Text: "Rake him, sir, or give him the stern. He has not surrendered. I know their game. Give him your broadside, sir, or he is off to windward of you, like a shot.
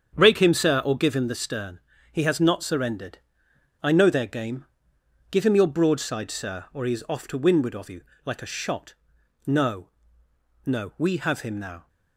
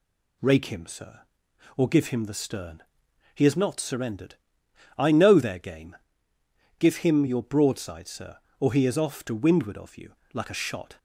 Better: second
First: starts louder than the rest; strong; until 1.2 s; 7.5 dB // goes on to say "No no we have him now"; strong; from 9.4 s on; 2.4 s long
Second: none

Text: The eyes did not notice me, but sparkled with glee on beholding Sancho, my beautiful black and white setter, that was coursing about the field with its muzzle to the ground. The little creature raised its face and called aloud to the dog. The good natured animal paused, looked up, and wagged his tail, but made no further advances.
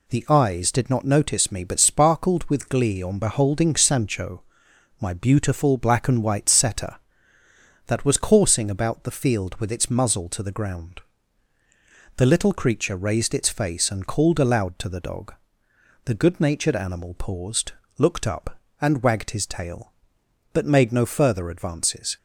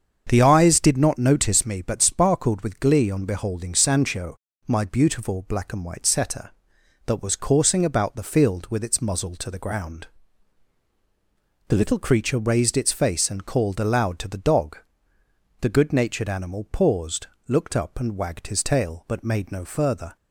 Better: first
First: none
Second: starts louder than the rest; until 1.2 s; 7 dB // stops before "advances"; at 20.1 s

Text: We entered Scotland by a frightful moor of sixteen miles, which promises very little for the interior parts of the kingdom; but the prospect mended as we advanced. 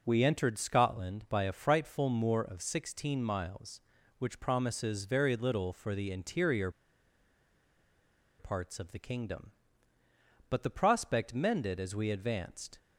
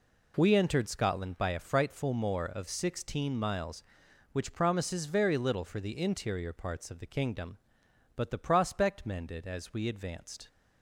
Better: second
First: pauses between "interior" and "parts"; strong; at 6.6 s; 1.7 s long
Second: none

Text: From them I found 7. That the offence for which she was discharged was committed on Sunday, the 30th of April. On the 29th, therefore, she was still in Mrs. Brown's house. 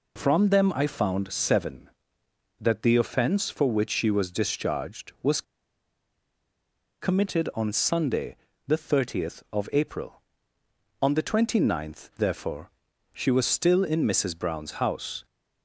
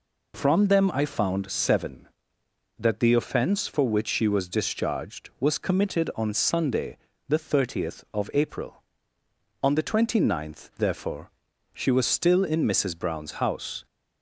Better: second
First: pauses between "was" and "committed"; strong; at 5.4 s; 1.5 s long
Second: none

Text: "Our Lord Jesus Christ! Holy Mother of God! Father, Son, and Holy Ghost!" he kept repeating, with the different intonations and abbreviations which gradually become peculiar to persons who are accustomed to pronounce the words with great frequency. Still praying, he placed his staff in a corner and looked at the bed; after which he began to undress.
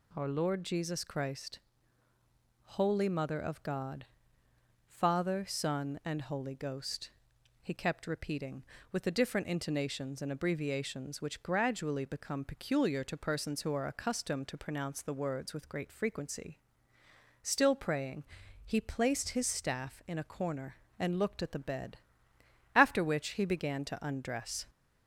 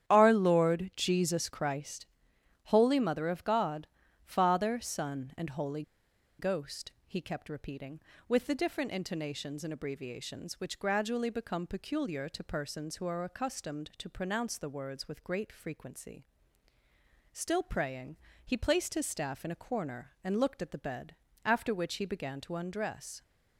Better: first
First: none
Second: starts louder than the rest; strong; until 1.1 s; 10 dB // pauses between "Holy" and "Ghost"; noticeable; at 5.8 s; 0.57 s long

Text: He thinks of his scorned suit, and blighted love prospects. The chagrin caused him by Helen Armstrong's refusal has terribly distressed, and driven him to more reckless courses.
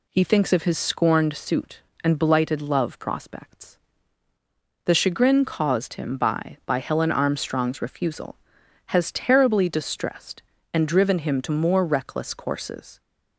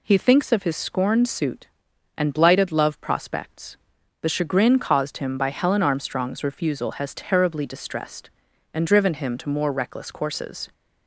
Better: second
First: says "by" twice; at 6.6 s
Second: none

